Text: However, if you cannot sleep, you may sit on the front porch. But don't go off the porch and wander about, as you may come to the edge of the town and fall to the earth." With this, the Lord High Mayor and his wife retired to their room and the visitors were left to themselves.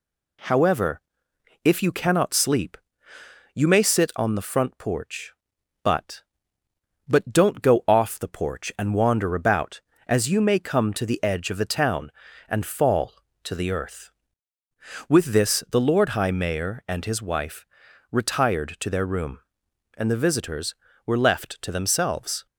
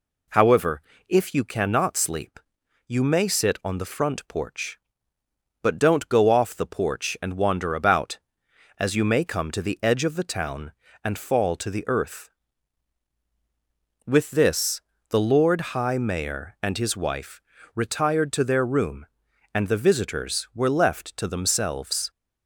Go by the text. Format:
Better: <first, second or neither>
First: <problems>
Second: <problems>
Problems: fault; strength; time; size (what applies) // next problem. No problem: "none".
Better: second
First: says "But" twice; at 7.0 s // pauses between "wife" and "retired"; noticeable; at 17.6 s; 0.46 s long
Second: pauses between "wife" and "retired"; slight; at 17.4 s; 0.32 s long